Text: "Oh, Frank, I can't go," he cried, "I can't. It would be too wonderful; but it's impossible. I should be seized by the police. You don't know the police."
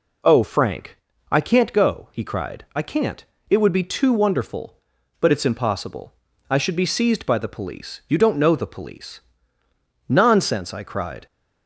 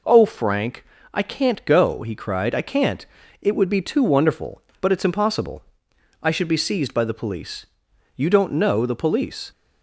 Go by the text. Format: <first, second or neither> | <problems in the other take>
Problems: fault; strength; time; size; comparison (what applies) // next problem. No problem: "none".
second | goes on to say "Nonsense I cried"; noticeable; from 10.0 s on; 1.1 s long